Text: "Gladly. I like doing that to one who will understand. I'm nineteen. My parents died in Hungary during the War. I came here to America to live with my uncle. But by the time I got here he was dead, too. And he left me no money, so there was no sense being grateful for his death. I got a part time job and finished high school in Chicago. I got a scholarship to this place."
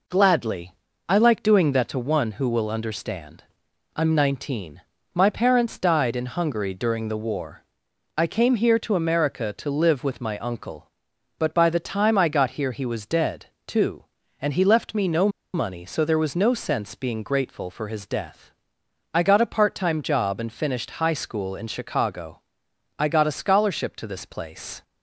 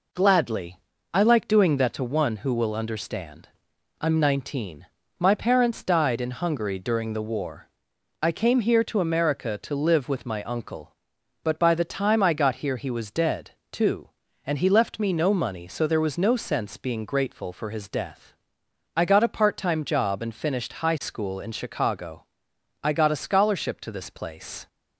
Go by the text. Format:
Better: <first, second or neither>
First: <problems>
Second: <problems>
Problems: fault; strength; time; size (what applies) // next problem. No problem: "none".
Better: second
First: pauses between "no" and "money"; slight; at 15.2 s; 0.25 s long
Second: none